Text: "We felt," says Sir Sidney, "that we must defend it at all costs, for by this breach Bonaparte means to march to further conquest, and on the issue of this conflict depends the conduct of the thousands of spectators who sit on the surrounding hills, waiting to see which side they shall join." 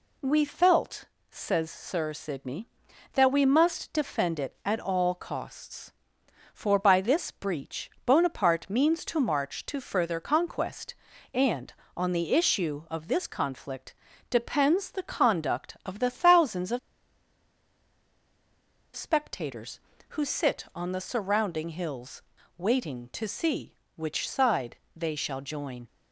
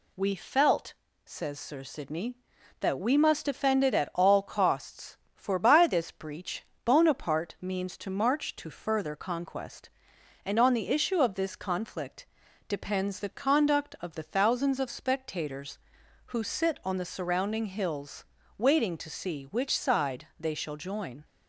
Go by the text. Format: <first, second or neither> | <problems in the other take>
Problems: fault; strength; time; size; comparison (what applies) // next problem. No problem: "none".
second | pauses between "breach" and "Bonaparte"; slight; at 7.8 s; 0.16 s long; slight in the second // pauses between "conflict" and "depends"; slight; at 13.9 s; 0.34 s long; also in the second // pauses between "of" and "spectators"; strong; at 16.7 s; 2.1 s long // pauses between "side" and "they"; slight; at 24.7 s; 0.20 s long